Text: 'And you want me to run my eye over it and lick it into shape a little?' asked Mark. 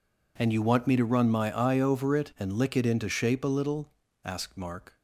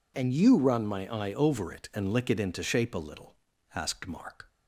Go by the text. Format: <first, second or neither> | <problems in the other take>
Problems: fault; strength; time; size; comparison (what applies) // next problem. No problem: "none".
first | skips "want me to"; at 0.5 s